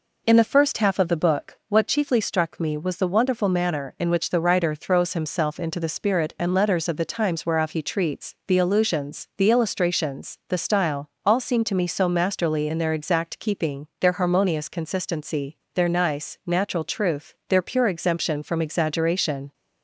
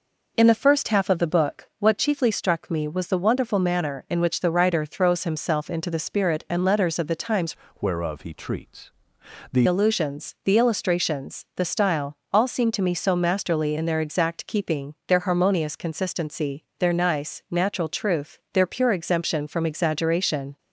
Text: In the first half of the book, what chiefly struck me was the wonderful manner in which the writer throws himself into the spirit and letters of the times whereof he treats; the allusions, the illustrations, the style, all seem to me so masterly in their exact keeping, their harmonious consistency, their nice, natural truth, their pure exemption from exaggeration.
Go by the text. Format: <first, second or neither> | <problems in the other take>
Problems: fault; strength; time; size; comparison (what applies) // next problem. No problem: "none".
first | changes voice from "whereof" to "the"; from 7.8 to 9.6 s; 1.8 s long